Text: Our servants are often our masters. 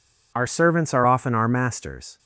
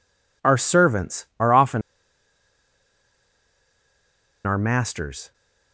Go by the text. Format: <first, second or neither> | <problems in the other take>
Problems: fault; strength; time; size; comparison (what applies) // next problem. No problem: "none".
first | pauses between "often" and "our"; strong; at 1.8 s; 2.6 s long